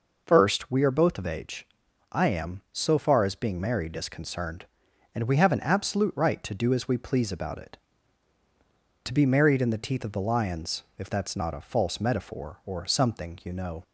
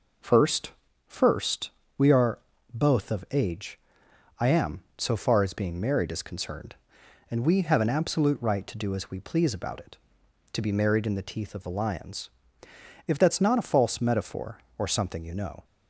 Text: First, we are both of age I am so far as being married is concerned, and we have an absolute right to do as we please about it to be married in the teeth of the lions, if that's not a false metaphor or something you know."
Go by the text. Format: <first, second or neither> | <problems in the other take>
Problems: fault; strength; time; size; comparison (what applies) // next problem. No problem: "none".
first | says "First" twice; at 1.0 s // pauses between "are" and "both"; slight; at 2.3 s; 0.34 s long // pauses between "age" and "I"; noticeable; at 3.7 s; 0.58 s long; also in the first